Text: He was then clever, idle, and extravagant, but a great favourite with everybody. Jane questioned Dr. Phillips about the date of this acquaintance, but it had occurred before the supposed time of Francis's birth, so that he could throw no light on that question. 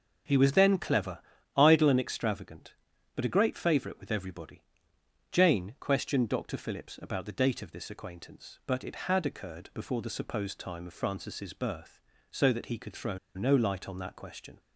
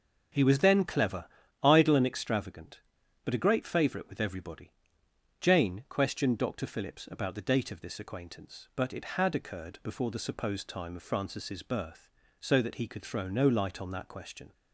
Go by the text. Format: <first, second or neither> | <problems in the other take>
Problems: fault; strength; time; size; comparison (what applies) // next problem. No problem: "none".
second | starts louder than the rest; until 1.6 s; 6.5 dB; also in the second // pauses between "throw" and "no"; slight; at 13.1 s; 0.18 s long